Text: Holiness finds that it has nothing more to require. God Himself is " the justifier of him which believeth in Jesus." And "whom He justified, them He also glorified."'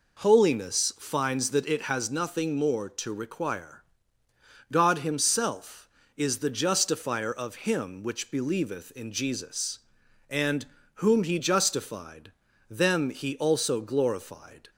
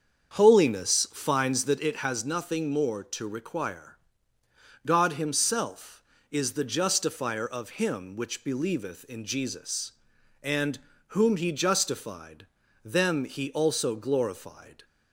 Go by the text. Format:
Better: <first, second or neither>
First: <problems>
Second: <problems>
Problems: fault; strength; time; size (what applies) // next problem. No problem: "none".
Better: first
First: pauses between "And" and "whom"; slight; at 10.6 s; 0.28 s long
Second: starts louder than the rest; strong; until 1.8 s; 7.5 dB // pauses between "And" and "whom"; slight; at 10.7 s; 0.28 s long